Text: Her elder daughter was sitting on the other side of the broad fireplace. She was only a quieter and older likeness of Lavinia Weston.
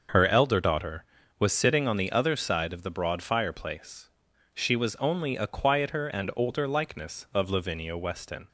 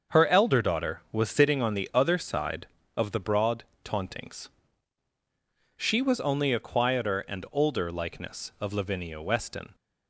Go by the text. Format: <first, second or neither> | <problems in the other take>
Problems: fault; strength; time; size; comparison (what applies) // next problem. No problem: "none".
first | starts louder than the rest; until 1.2 s; 6.5 dB; also in the first // says "tauntings" for "fireplace"; at 3.8 s